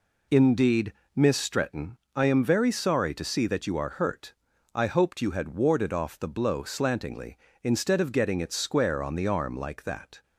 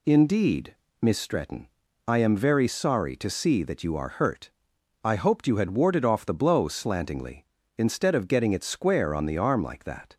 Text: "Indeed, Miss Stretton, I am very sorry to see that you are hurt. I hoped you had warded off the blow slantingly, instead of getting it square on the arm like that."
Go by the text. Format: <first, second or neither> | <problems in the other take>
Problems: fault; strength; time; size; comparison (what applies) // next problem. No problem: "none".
neither | none